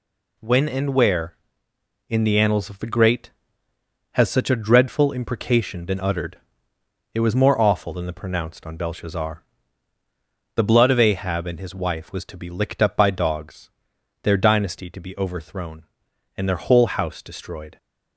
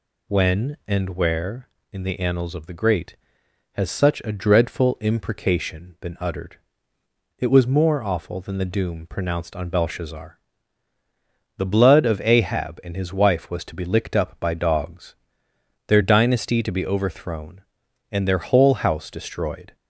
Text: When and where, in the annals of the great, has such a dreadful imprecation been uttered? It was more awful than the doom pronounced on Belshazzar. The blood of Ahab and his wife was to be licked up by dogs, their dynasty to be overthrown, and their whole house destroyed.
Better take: second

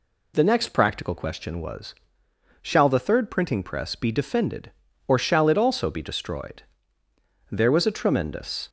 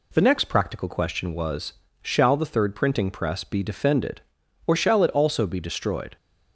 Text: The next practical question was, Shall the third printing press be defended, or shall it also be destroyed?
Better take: second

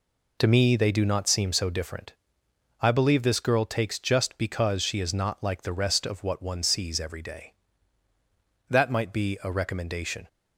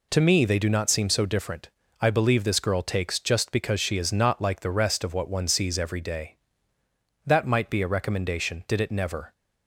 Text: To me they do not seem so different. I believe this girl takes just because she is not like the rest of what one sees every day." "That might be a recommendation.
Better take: first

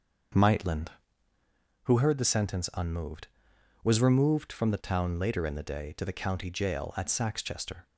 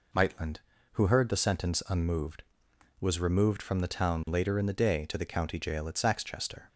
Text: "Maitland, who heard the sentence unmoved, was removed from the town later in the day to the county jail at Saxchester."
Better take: second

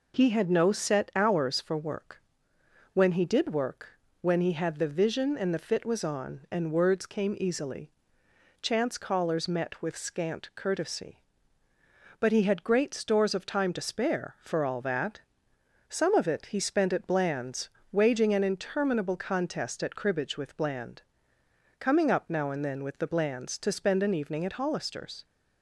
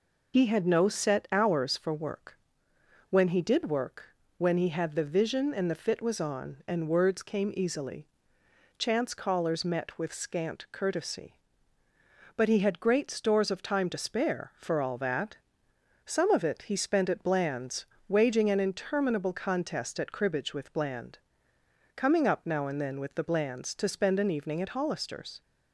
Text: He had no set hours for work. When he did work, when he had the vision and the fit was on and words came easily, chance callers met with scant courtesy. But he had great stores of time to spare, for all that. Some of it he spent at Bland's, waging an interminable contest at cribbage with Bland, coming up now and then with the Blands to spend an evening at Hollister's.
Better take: first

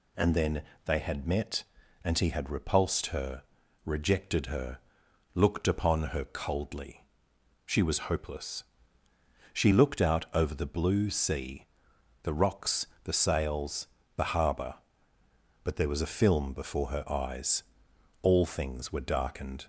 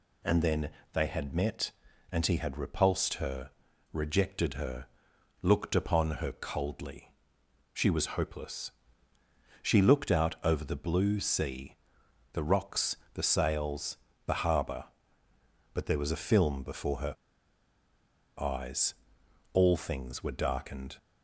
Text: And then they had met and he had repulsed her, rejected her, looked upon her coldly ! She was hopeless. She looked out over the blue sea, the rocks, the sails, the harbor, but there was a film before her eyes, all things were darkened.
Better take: first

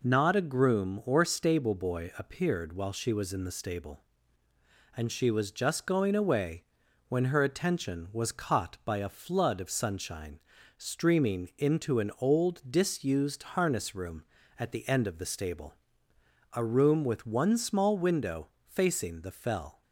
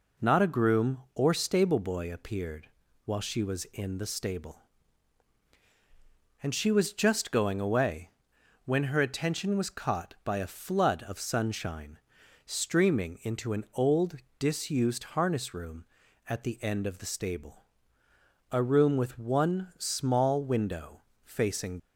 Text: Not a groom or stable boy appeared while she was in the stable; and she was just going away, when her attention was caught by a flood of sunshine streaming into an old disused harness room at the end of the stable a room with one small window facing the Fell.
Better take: first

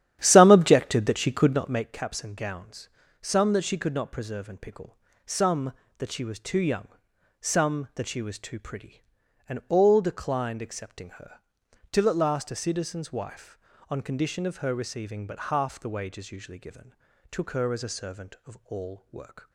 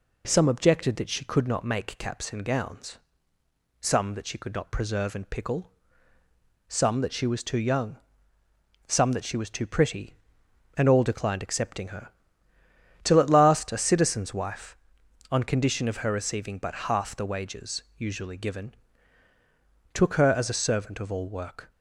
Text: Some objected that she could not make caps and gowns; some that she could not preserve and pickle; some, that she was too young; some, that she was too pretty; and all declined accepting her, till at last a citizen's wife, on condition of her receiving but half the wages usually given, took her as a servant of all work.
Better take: second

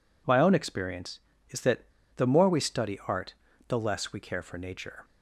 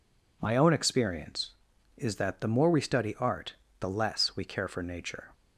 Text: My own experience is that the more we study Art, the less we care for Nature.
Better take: second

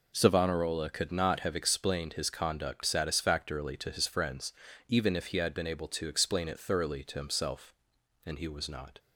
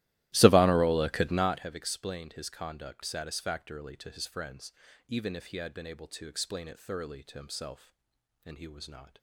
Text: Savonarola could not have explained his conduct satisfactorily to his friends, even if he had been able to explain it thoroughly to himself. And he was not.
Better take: first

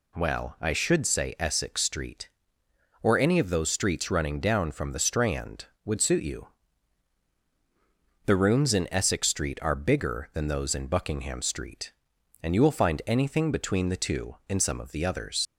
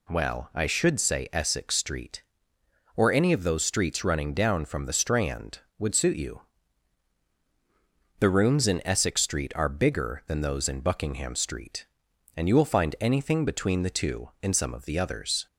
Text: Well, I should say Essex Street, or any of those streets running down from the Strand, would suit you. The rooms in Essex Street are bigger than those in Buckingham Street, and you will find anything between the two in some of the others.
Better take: second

